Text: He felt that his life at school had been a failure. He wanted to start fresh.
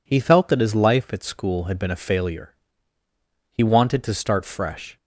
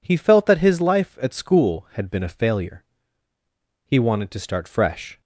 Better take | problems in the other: neither | none

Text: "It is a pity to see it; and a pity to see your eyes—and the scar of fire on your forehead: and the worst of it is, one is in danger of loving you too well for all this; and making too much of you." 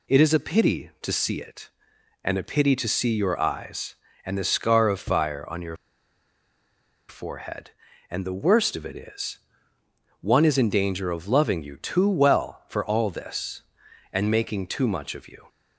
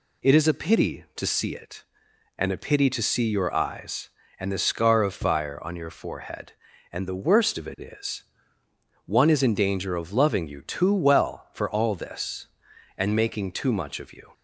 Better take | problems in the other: second | pauses between "your" and "forehead"; strong; at 5.7 s; 1.3 s long

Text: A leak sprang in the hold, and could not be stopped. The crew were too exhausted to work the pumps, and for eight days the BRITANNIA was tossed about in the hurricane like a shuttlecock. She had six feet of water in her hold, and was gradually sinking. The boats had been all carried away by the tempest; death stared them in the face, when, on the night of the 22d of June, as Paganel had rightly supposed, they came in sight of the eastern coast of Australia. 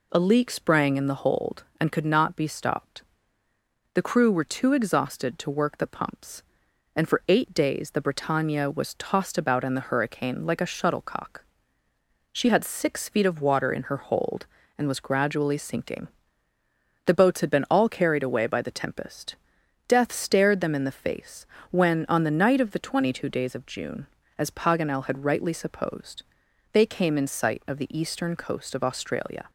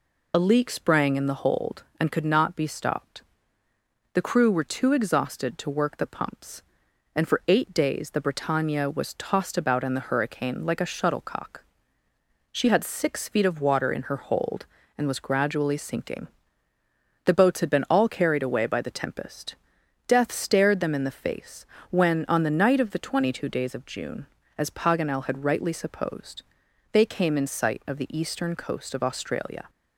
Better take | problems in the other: first | loses the start of "A"; at 0.3 s; 30 ms

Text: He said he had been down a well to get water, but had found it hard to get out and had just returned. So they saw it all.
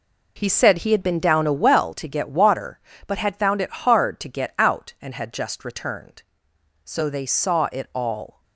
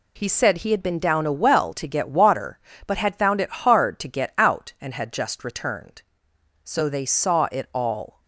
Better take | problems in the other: second | starts louder than the rest; noticeable; until 1.9 s; 4 dB

